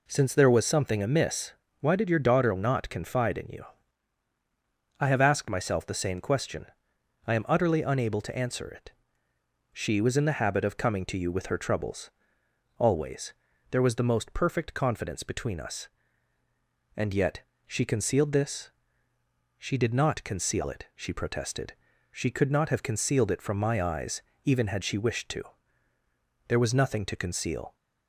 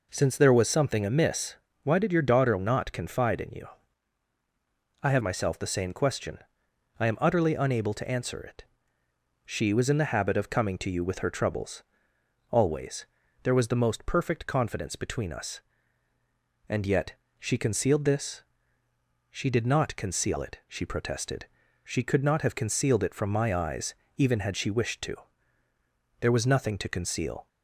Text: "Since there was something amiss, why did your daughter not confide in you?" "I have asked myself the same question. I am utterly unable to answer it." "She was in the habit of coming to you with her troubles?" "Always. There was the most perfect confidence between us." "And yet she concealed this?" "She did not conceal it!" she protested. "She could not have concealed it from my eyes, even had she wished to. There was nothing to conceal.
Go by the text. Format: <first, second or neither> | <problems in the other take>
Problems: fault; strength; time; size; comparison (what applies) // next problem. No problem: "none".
first | skips "asked"; at 5.2 s // pauses between "yet" and "she"; slight; at 17.1 s; 0.24 s long; slight in the first